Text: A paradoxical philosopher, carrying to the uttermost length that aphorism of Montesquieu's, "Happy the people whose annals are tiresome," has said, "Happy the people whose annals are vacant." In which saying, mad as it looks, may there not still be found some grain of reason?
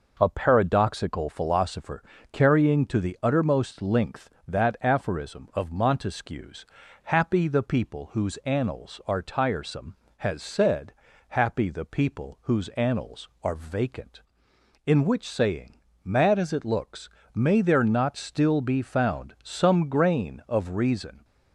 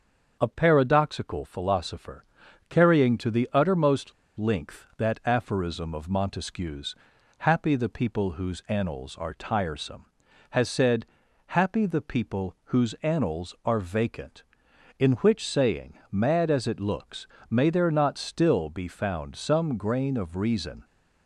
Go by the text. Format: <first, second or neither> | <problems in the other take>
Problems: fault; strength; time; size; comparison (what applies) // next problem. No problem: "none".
first | starts louder than the rest; until 1.4 s; 6.5 dB // pauses between "uttermost" and "length"; slight; at 4.1 s; 0.25 s long